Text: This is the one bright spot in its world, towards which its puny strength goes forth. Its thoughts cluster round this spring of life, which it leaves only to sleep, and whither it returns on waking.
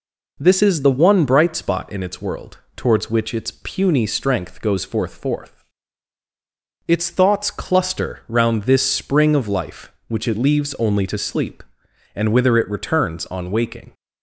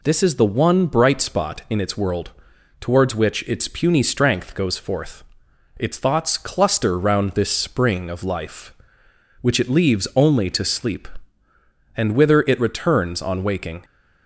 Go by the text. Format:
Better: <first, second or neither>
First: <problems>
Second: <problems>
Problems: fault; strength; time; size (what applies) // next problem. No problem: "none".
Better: second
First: says "forth" twice; at 5.1 s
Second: none